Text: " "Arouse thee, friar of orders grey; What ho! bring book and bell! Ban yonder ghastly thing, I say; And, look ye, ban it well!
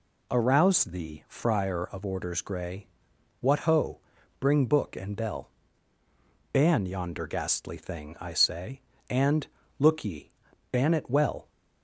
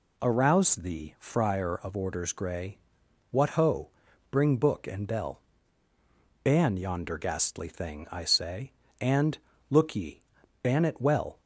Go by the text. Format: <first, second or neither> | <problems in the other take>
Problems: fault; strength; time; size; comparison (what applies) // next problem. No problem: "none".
neither | none